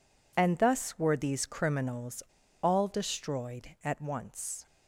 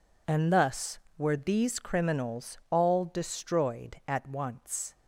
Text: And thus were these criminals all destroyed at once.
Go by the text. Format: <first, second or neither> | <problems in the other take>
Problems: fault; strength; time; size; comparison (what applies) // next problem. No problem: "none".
second | pauses between "criminals" and "all"; at 2.1 s; 0.41 s long